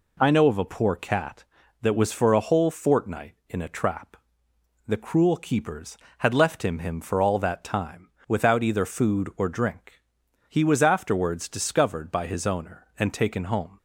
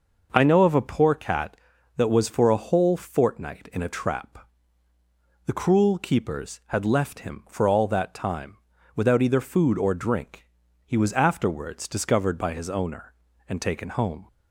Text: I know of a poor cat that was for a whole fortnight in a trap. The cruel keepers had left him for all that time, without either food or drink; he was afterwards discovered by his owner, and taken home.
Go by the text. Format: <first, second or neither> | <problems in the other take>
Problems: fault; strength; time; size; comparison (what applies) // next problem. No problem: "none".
second | says "him" twice; at 6.7 s